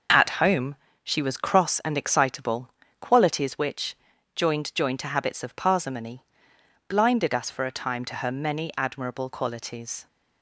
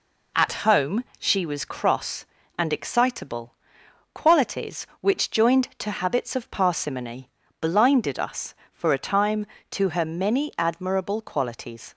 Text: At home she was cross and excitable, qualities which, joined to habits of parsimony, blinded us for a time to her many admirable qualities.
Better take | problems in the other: second | pauses between "home" and "she"; slight; at 0.7 s; 0.30 s long; slight in the second // says "joined" twice; at 4.7 s

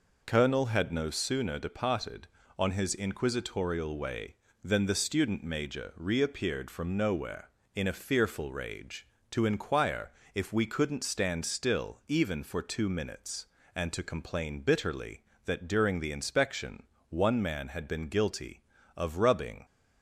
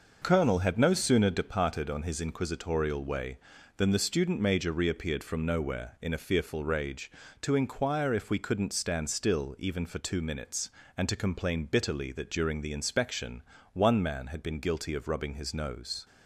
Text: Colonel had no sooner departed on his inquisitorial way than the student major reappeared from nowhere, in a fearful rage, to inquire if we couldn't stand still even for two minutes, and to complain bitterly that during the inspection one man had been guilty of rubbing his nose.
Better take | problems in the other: second | pauses between "inquire" and "if"; slight; at 10.1 s; 0.24 s long // pauses between "inspection" and "one"; slight; at 16.8 s; 0.26 s long; slight in the second // stops before "his nose"; at 19.6 s

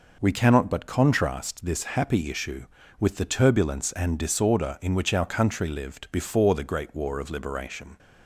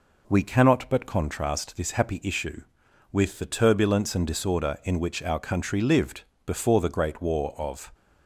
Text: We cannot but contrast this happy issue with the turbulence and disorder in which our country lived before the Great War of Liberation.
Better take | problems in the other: first | pauses between "lived" and "before"; slight; at 6.2 s; 0.24 s long // stops before "Liberation"; at 7.9 s

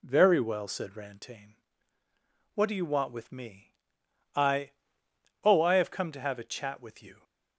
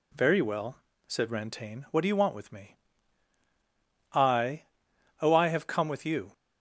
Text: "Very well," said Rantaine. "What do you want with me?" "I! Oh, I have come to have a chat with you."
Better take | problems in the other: first | skips "to have a chat"; at 5.8 s

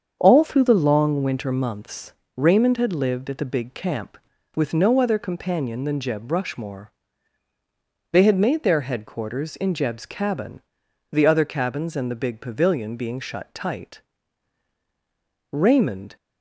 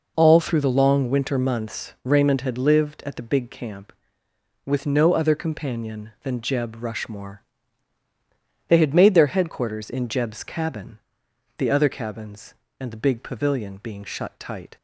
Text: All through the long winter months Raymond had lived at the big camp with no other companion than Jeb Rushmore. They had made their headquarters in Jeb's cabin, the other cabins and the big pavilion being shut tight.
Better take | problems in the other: second | starts louder than the rest; strong; until 1.2 s; 7.5 dB // pauses between "months" and "Raymond"; slight; at 2.1 s; 0.22 s long // goes on to say "Raymond"; noticeable; from 15.5 s on; 0.64 s long

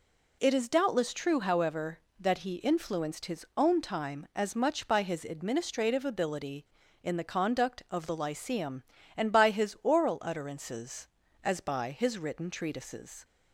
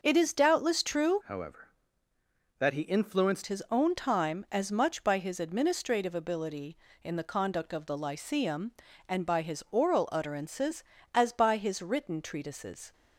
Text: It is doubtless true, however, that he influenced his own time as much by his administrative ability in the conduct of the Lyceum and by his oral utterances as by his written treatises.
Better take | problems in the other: first | starts louder than the rest; noticeable; until 1.0 s; 6 dB // changes voice from "however" to "influenced"; from 1.2 to 3.4 s; 2.2 s long

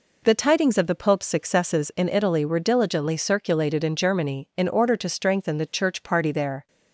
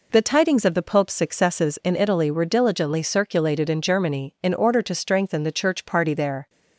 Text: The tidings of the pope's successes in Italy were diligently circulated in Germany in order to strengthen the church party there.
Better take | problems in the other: neither | none

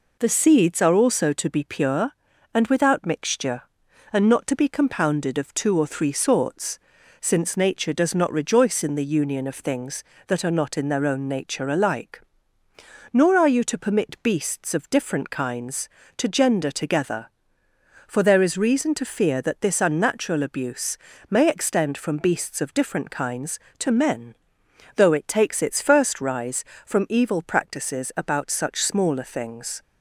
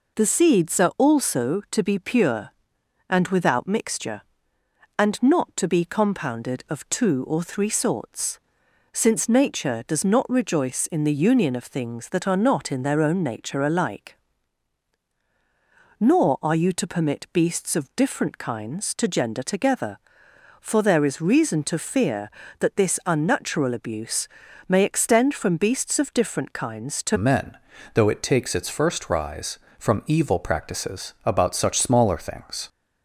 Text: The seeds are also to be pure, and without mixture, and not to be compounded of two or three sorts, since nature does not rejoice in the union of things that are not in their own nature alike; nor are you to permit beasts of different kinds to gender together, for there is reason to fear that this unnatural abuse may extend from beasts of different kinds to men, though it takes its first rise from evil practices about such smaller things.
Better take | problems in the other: first | pauses between "abuse" and "may"; at 24.2 s; 0.42 s long; slight in the first // changes voice at "men"; from 27.1 s on; 5.5 s long

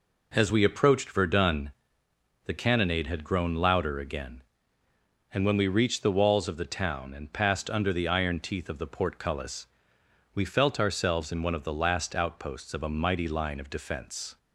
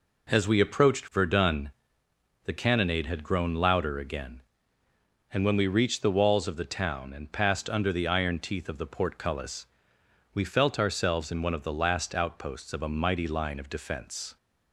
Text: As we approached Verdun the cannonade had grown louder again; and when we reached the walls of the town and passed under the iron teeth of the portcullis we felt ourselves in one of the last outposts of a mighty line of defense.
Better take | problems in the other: neither | pauses between "Verdun" and "the"; noticeable; the same in both // pauses between "portcullis" and "we"; noticeable; the same in both

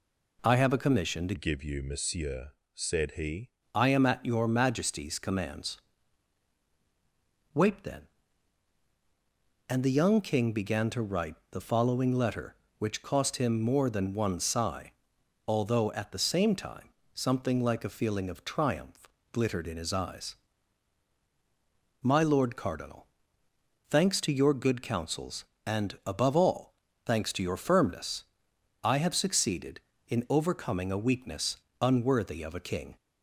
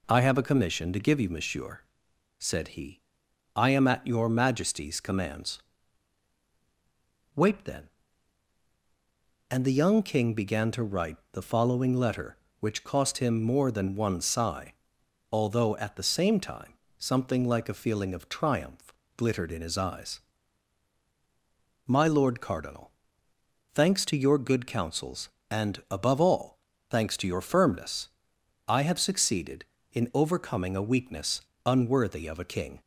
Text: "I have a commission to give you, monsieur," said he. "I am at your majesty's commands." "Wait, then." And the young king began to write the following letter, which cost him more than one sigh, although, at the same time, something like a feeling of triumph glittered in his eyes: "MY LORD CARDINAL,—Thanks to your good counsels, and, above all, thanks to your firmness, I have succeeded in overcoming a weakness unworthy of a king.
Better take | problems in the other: second | changes voice from "give" to "he"; from 1.3 to 3.4 s; 2.1 s long // pauses between "triumph" and "glittered"; slight; at 19.0 s; 0.24 s long; slight in the second // pauses between "weakness" and "unworthy"; slight; at 31.5 s; 0.22 s long; slight in the second

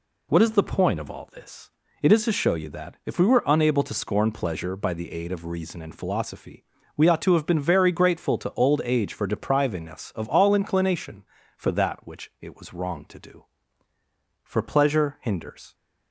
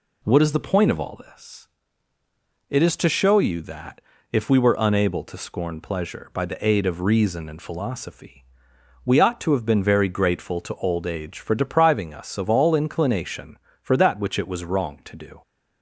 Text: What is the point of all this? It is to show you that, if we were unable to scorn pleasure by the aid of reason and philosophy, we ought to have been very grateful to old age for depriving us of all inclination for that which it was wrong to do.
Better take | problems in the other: second | goes on to say "For pleasure hinders"; noticeable; from 14.4 s on; 1.3 s long

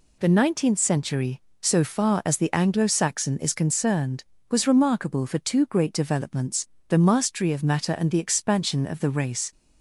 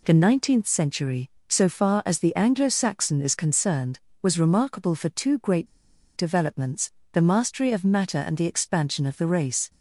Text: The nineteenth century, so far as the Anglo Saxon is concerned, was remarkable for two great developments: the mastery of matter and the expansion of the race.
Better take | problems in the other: first | pauses between "great" and "developments"; noticeable; at 5.6 s; 0.50 s long

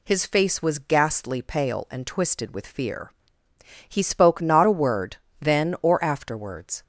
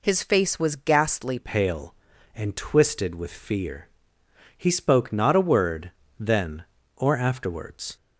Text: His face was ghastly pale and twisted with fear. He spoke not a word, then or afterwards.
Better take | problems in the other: first | changes voice at "pale"; from 1.3 s on; 6.6 s long

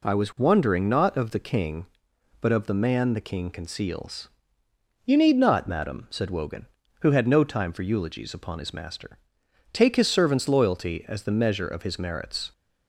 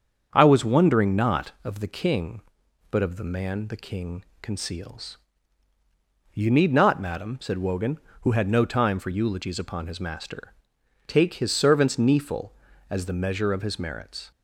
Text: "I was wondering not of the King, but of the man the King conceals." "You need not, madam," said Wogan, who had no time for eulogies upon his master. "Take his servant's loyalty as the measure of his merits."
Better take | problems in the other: first | starts louder than the rest; strong; until 1.3 s; 7.5 dB // pauses between "King" and "conceals"; slight; at 4.2 s; 0.16 s long // says "kneeful" for "loyalty"; at 11.9 s

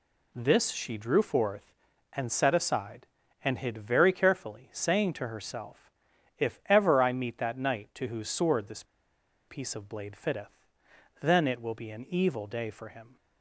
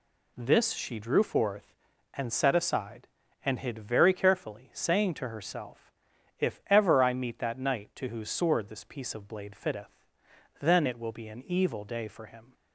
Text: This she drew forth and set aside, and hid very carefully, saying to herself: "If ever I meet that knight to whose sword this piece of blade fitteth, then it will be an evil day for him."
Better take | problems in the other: second | pauses between "this" and "piece"; noticeable; at 8.8 s; 0.63 s long

